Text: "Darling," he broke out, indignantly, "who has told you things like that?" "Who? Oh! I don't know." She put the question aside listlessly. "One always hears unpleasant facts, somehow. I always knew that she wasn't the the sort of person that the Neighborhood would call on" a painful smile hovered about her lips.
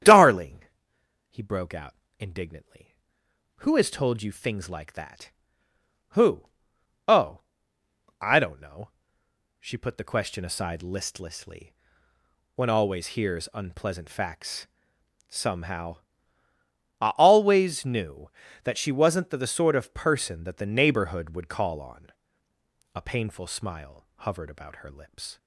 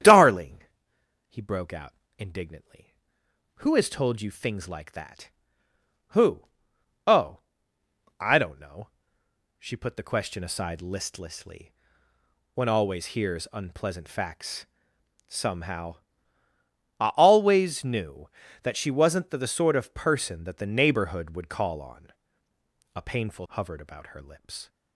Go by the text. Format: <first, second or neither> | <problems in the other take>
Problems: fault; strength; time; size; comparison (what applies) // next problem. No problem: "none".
first | starts louder than the rest; strong; until 1.6 s; 9.5 dB; strong in the first // pauses between "on" and "a"; noticeable; at 22.1 s; 0.84 s long; noticeable in the first // skips "smile"; at 23.4 s